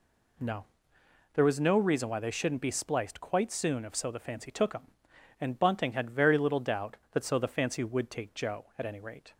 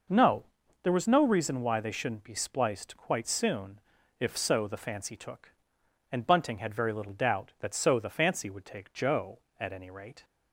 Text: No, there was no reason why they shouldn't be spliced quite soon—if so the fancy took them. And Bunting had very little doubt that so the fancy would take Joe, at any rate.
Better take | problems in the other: first | skips "them"; at 5.8 s

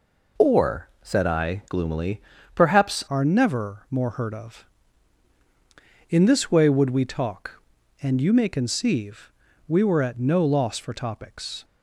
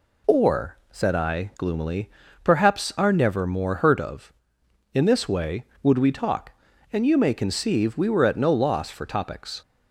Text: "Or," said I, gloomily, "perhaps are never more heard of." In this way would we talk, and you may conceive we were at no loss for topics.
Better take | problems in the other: second | changes voice at "are"; from 3.0 s on; 8.6 s long // pauses between "conceive" and "we"; slight; at 9.3 s; 0.36 s long

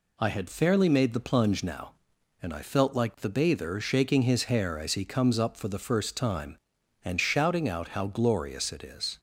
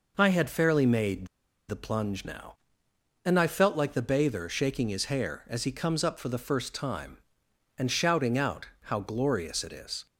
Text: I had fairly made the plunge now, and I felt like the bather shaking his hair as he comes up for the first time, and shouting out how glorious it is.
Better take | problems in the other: first | pauses between "made" and "the"; at 1.2 s; 0.41 s long // pauses between "out" and "how"; slight; at 8.6 s; 0.18 s long

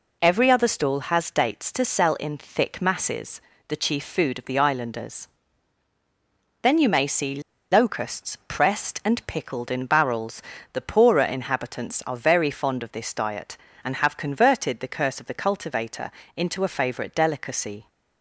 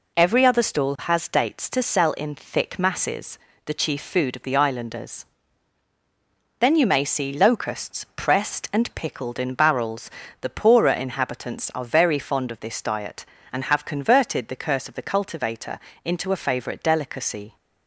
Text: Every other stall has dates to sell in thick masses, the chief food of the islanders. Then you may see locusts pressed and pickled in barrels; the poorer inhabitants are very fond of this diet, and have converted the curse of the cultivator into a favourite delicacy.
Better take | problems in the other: second | pauses between "see" and "locusts"; slight; at 7.4 s; 0.31 s long // pauses between "cultivator" and "into"; slight; at 16.0 s; 0.24 s long; slight in the second

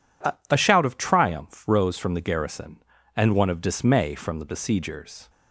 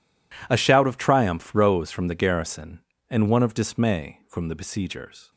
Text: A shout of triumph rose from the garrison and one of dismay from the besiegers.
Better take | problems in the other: second | says "A" twice; at 0.5 s

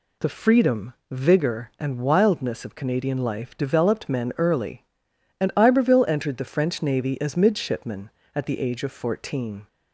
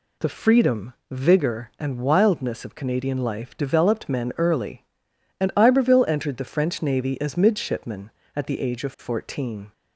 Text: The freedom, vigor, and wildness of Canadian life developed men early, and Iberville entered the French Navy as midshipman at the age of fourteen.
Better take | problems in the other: neither | none

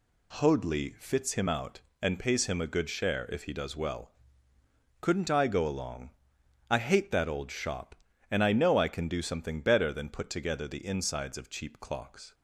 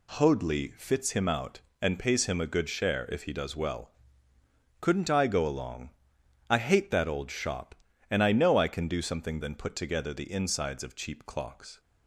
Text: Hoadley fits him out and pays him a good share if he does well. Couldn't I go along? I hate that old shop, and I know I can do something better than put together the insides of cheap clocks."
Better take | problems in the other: first | skips "better"; at 9.4 s

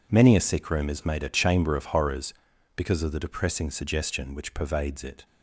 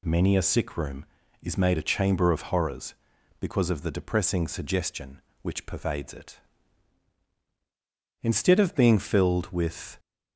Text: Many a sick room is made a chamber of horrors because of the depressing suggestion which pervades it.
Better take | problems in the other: first | goes on to say "Instead of being filled with"; strong; from 8.2 s on; 1.7 s long

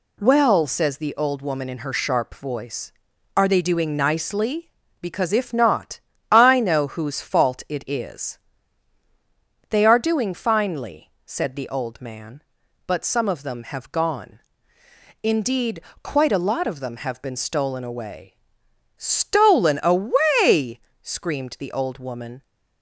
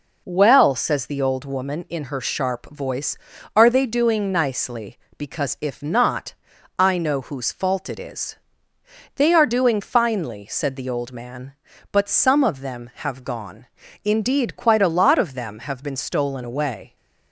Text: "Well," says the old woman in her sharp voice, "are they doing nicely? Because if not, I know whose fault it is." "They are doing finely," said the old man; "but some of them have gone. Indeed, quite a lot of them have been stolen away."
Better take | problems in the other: second | goes on to say "Stolen away screamed the old woman"; strong; from 18.9 s on; 3.4 s long

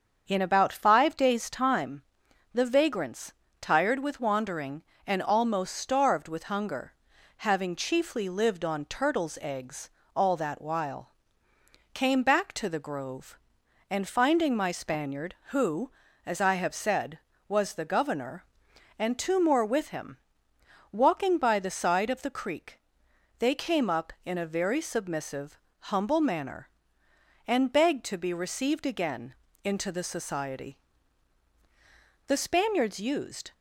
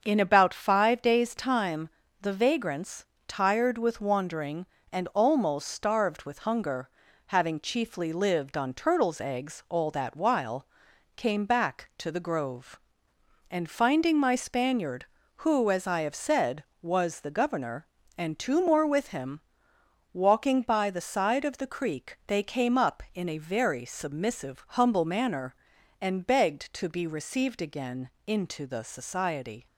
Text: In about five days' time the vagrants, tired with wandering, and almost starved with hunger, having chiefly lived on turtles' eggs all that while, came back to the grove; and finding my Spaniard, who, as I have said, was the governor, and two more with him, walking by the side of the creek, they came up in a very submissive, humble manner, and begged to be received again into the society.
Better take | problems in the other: second | starts louder than the rest; until 1.2 s; 7 dB; also in the second // pauses between "time" and "the"; noticeable; at 2.0 s; 0.50 s long; slight in the second // pauses between "eggs" and "all"; slight; at 9.8 s; 0.26 s long // pauses between "again" and "into"; slight; at 29.3 s; 0.30 s long; slight in the second // goes on to say "The Spaniards used"; noticeable; from 32.2 s on; 1.2 s long

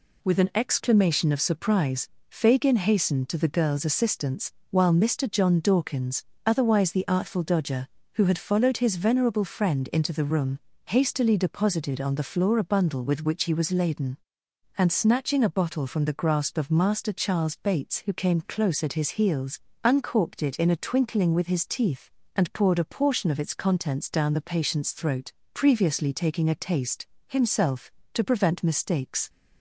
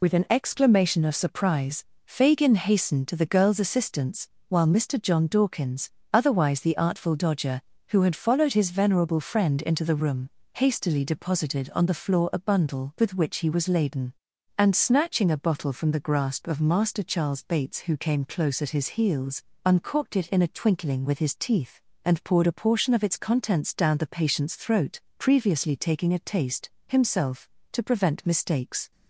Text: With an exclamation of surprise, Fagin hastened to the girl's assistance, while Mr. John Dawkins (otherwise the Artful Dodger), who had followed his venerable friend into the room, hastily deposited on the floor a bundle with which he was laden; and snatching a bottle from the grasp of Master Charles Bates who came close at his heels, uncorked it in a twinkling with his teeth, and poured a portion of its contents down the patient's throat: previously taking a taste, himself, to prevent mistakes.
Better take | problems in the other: first | loses the start of "With"; at 0.0 s; 45 ms

